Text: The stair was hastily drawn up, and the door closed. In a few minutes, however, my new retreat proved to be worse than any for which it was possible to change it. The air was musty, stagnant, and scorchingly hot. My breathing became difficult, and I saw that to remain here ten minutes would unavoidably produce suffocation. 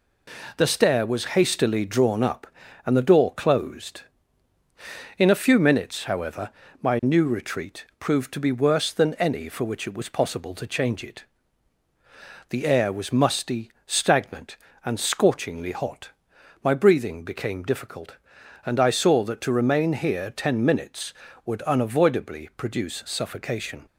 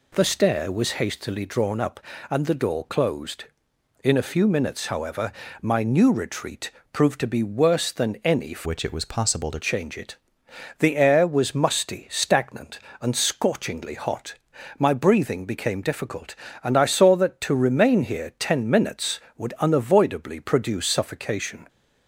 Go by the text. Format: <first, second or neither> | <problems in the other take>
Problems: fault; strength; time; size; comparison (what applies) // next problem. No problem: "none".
first | pauses between "retreat" and "proved"; slight; at 6.6 s; 0.22 s long // changes voice from "which" to "to"; from 8.6 to 9.5 s; 0.9 s long